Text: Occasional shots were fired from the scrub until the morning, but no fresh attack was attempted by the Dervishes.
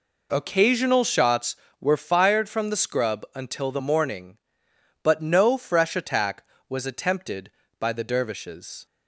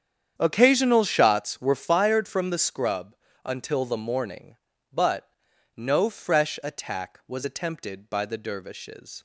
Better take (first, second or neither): first